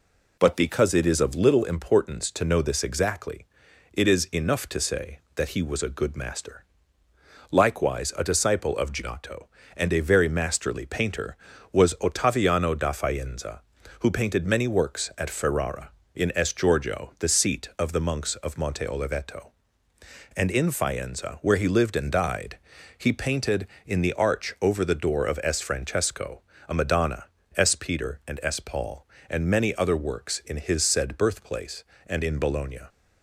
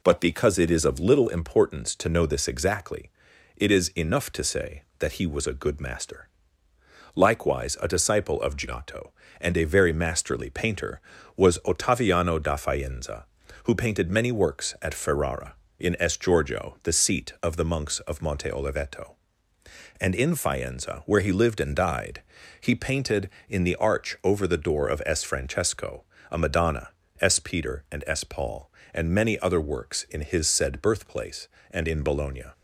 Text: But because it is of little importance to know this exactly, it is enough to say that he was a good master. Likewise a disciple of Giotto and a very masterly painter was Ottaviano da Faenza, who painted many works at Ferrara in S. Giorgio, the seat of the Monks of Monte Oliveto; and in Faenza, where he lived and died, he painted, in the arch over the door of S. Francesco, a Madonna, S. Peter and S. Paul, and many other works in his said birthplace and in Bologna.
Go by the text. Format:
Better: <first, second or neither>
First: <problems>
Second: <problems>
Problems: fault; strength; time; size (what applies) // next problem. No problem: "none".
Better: neither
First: none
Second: none